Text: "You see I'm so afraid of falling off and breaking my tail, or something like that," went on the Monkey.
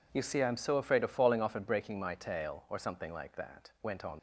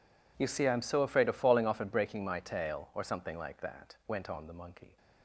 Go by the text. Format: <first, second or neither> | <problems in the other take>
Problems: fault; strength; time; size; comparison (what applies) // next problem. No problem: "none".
second | stops before "the Monkey"; at 4.1 s